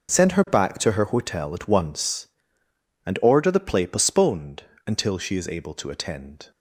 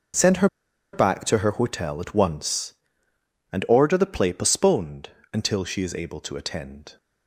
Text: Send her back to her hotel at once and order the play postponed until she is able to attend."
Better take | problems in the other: first | starts louder than the rest; noticeable; until 1.6 s; 6 dB; noticeable in the first // pauses between "her" and "back"; noticeable; at 0.4 s; 0.46 s long // pauses between "postponed" and "until"; slight; at 5.0 s; 0.24 s long; slight in the first

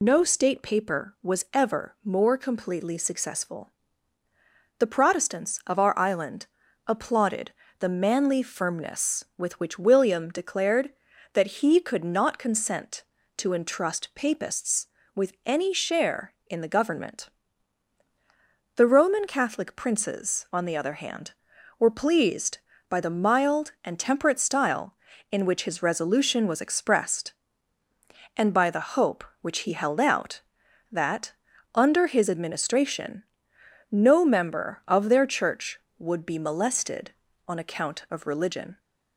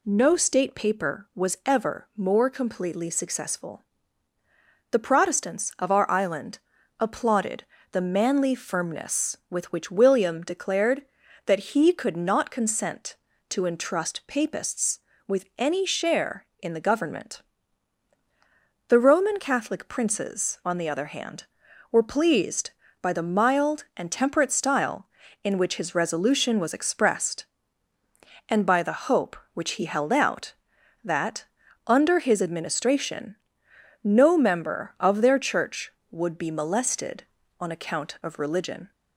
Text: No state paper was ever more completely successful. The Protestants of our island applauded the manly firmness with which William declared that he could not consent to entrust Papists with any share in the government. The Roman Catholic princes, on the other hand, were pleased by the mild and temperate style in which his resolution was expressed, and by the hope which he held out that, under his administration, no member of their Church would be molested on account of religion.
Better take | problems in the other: second | loses the start of "No"; at 0.0 s; 85 ms // pauses between "island" and "applauded"; at 6.4 s; 0.42 s long; also in the second // pauses between "applauded" and "the"; slight; at 7.5 s; 0.26 s long; slight in the second

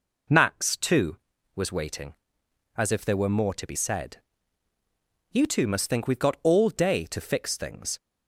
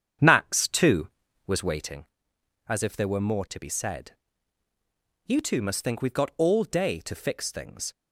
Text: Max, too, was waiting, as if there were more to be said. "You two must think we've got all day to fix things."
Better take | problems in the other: first | starts louder than the rest; strong; until 2.0 s; 8 dB

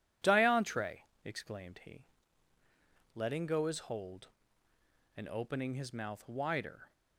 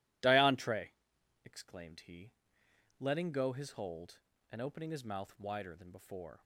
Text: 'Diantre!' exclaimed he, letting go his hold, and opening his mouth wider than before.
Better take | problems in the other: second | stops before "than before"; at 6.9 s

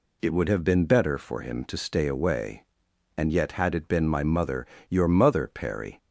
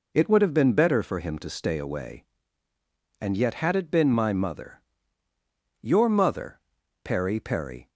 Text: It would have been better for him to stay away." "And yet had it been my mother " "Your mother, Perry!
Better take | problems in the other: first | says "Perry" twice; at 7.3 s

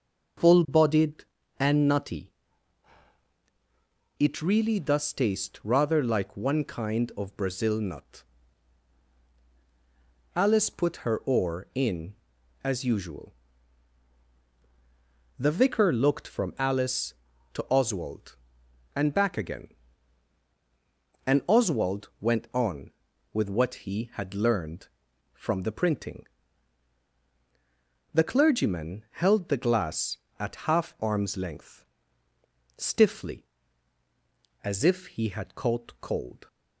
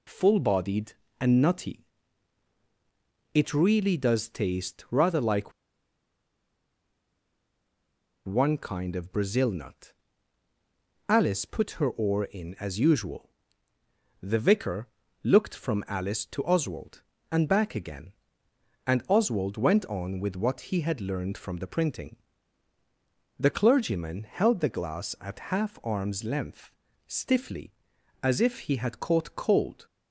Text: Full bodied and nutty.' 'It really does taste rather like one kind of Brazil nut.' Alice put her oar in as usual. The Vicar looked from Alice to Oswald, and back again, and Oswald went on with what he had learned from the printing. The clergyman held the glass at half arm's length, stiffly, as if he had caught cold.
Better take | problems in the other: first | pauses between "like" and "one"; strong; at 5.5 s; 2.7 s long // pauses between "Vicar" and "looked"; slight; at 14.8 s; 0.34 s long

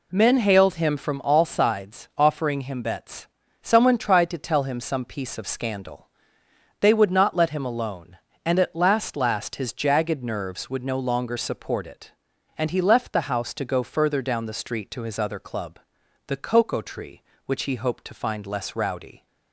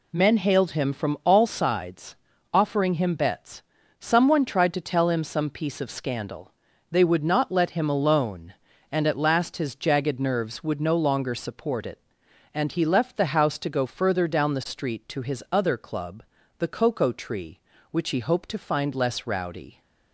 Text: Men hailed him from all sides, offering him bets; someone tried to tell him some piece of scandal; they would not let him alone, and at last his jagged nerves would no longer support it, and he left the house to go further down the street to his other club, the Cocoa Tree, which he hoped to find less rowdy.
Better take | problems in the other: second | says "last" twice; at 9.1 s

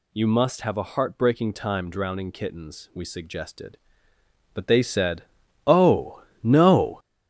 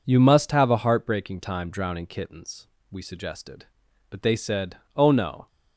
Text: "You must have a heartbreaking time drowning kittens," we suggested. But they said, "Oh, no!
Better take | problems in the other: second | gets louder; throughout; 7 dB

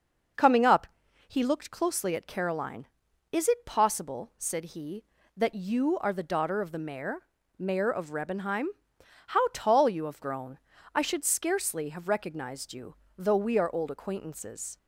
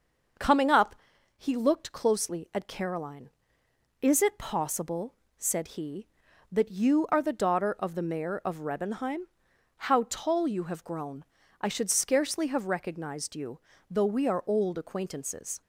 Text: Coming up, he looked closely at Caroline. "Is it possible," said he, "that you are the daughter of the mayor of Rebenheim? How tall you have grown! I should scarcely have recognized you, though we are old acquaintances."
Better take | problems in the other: second | starts louder than the rest; until 1.7 s; 6 dB; also in the second // says "mayor" twice; at 7.5 s

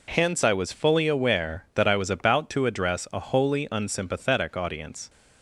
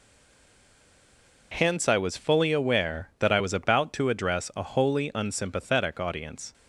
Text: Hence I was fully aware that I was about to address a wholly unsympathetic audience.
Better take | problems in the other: first | stays silent before the first word; noticeable; until 1.5 s; 1.5 s long

